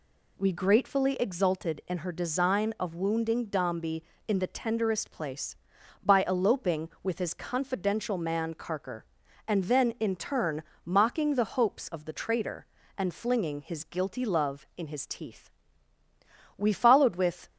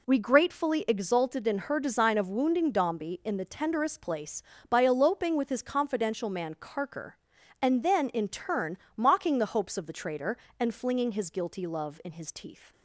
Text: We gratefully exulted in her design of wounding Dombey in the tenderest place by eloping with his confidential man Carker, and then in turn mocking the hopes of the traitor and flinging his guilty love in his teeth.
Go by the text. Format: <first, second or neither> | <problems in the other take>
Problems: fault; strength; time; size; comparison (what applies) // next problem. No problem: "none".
second | pauses between "turn" and "mocking"; slight; at 10.6 s; 0.22 s long; slight in the second // goes on to say "We followed with"; noticeable; from 16.5 s on; 0.92 s long